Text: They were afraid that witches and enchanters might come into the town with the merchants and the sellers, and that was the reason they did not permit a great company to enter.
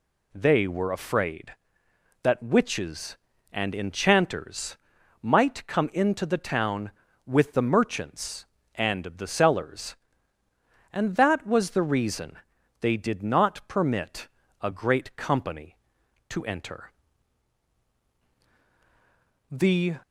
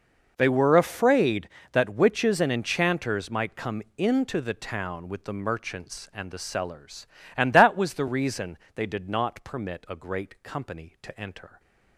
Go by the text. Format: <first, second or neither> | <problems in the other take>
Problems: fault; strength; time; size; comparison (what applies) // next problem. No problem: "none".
second | pauses between "enchanters" and "might"; at 4.7 s; 0.44 s long // pauses between "reason" and "they"; at 12.3 s; 0.44 s long; slight in the second // pauses between "permit" and "a"; slight; at 14.2 s; 0.32 s long // goes on to say "The"; slight; from 19.4 s on; 0.48 s long